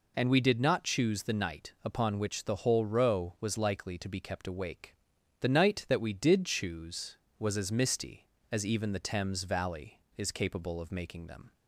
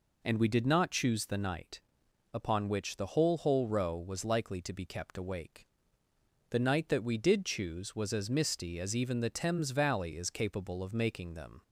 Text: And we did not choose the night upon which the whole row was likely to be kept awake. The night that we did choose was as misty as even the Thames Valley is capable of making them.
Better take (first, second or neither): first